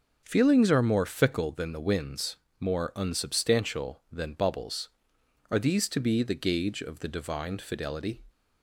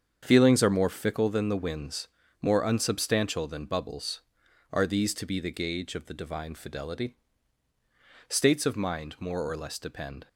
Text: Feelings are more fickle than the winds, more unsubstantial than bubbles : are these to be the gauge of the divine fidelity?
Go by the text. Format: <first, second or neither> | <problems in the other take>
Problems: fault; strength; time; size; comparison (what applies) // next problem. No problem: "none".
first | starts louder than the rest; strong; until 1.2 s; 7.5 dB; noticeable in the first // goes on to say "States of mind more or less depend"; strong; from 8.2 s on; 1.9 s long